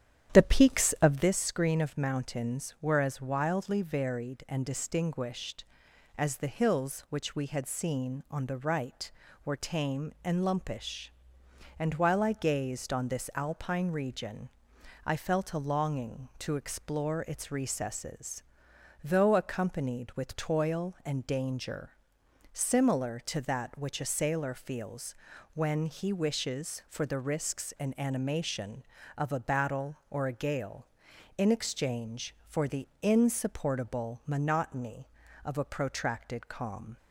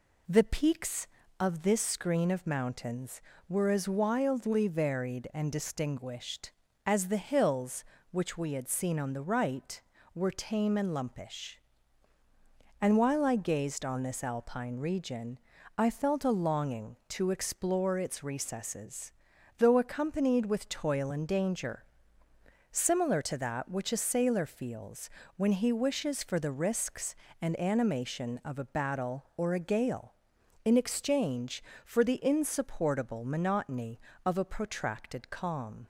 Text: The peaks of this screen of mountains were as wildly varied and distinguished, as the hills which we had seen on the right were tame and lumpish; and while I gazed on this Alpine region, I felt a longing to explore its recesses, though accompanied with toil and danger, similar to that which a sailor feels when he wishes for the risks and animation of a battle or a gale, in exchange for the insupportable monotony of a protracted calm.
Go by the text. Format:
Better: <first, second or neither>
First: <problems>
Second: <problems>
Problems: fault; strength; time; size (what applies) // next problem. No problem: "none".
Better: second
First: starts louder than the rest; strong; until 1.3 s; 10.5 dB // pauses between "feels" and "when"; at 25.1 s; 0.40 s long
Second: pauses between "feels" and "when"; slight; at 25.1 s; 0.26 s long